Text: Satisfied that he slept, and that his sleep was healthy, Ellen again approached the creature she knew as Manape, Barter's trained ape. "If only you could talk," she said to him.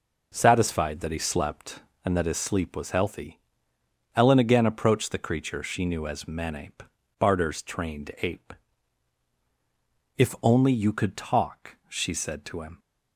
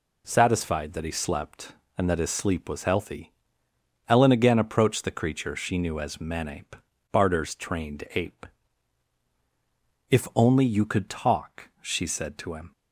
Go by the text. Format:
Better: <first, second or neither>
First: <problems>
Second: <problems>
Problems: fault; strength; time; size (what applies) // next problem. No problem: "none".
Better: second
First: starts louder than the rest; noticeable; until 2.2 s; 4.5 dB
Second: none